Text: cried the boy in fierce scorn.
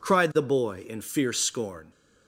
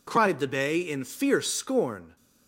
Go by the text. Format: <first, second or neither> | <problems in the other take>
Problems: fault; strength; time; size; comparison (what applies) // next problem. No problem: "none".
first | says "bay" for "boy"; at 0.4 s